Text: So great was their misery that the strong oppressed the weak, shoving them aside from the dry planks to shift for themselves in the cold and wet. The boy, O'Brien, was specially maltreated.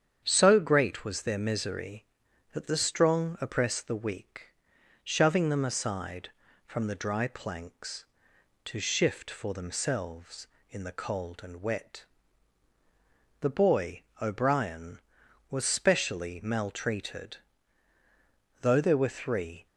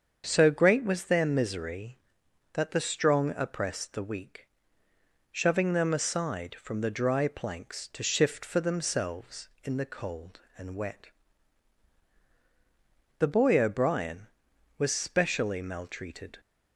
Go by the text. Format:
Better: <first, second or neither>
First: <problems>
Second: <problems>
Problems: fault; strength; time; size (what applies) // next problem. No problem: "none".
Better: second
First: starts louder than the rest; strong; until 1.2 s; 8.5 dB // goes on to say "Though there were three"; noticeable; from 18.6 s on; 1.0 s long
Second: starts louder than the rest; until 1.2 s; 7 dB